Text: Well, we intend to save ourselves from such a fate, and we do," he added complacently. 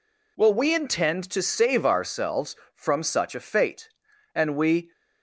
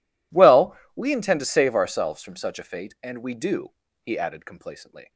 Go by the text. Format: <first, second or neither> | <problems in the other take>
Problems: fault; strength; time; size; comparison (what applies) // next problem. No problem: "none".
second | stops before "do he added complacently"; at 4.9 s